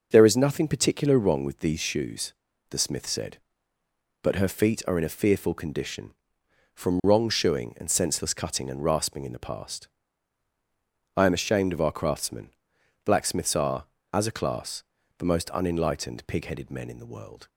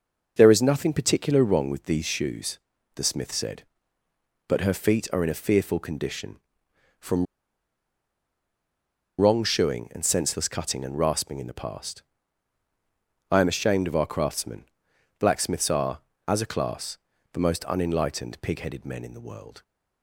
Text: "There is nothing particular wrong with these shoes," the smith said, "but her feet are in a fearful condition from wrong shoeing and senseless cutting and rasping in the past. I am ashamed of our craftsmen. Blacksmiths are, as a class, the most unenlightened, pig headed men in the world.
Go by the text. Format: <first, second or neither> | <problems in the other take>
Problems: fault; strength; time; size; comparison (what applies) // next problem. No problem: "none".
first | pauses between "from" and "wrong"; strong; at 7.2 s; 1.9 s long